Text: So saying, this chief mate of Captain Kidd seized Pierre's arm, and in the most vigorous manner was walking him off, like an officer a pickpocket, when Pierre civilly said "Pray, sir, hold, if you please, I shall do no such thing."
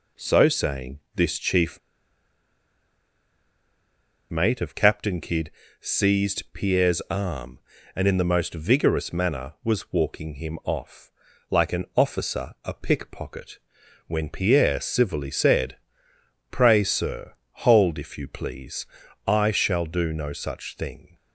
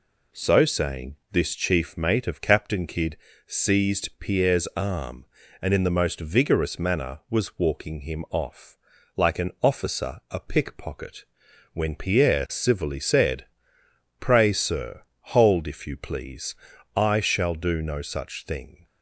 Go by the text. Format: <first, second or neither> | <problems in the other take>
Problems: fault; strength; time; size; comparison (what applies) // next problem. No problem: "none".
second | pauses between "chief" and "mate"; strong; at 1.7 s; 2.5 s long // pauses between "Kidd" and "seized"; slight; at 5.5 s; 0.30 s long; slight in the second // pauses between "said" and "Pray"; noticeable; at 15.7 s; 0.74 s long; noticeable in the second